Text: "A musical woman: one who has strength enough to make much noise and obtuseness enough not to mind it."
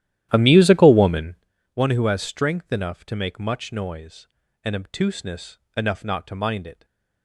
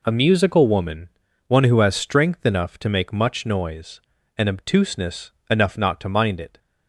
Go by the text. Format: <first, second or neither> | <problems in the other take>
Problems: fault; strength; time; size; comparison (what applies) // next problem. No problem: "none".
second | starts louder than the rest; strong; until 1.5 s; 12.5 dB // pauses between "obtuseness" and "enough"; slight; at 5.5 s; 0.18 s long; slight in the second // stays silent after the last word; slight; from 6.7 s on; 0.5 s long